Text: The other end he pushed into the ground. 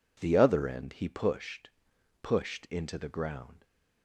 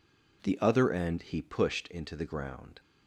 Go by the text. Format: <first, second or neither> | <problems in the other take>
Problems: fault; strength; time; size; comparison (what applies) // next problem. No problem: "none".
second | says "pushed" twice; at 2.2 s